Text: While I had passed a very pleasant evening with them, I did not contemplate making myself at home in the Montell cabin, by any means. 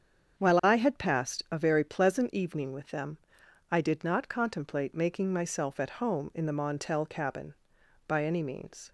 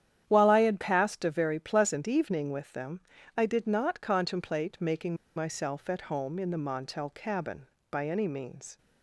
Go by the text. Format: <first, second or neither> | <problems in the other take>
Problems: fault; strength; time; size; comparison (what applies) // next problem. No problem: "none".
first | starts louder than the rest; strong; until 1.2 s; 10 dB; strong in the first // pauses between "making" and "myself"; slight; at 5.1 s; 0.22 s long